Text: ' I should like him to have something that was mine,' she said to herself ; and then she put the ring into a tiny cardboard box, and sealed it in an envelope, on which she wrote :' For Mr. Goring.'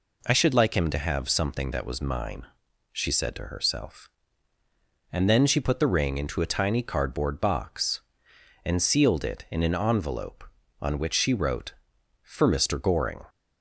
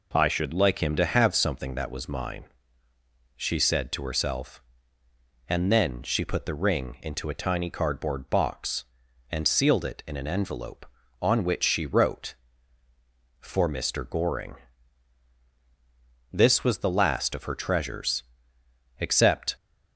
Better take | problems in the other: first | goes on to say "This was the last of her treasures except"; strong; from 16.3 s on; 3.2 s long

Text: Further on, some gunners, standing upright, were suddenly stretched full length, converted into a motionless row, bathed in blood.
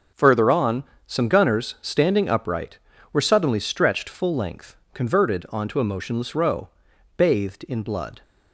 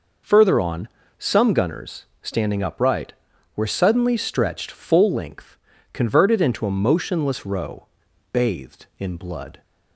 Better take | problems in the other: second | starts louder than the rest; noticeable; until 1.3 s; 6 dB // says "onto" for "into"; at 5.4 s

